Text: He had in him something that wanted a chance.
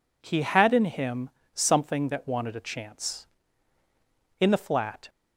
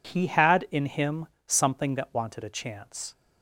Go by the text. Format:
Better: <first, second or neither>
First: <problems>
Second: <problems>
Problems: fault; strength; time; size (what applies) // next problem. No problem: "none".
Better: second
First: pauses between "him" and "something"; slight; at 1.2 s; 0.23 s long // goes on to say "In the flat"; noticeable; from 4.4 s on; 0.68 s long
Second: pauses between "him" and "something"; slight; at 1.2 s; 0.18 s long